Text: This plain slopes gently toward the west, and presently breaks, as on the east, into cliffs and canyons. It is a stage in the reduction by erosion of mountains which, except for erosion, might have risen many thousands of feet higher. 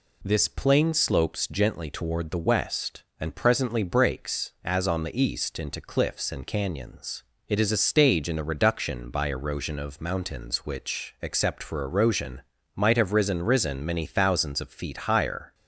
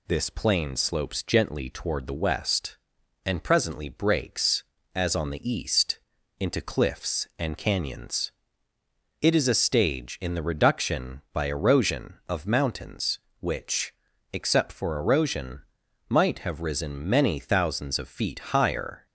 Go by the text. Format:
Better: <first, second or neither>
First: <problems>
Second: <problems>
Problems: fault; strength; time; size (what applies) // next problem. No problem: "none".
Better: second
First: says "risen" twice; at 13.4 s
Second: none